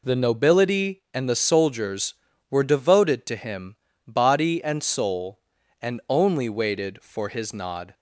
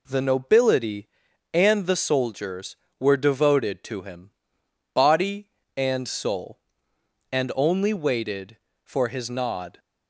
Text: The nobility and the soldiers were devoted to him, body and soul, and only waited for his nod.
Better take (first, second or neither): neither